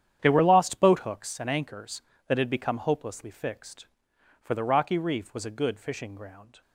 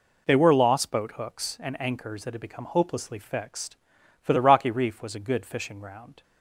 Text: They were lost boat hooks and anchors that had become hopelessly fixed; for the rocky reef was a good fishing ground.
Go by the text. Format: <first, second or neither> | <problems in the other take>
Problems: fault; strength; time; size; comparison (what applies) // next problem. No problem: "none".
second | gets quieter; strong; throughout; 13.5 dB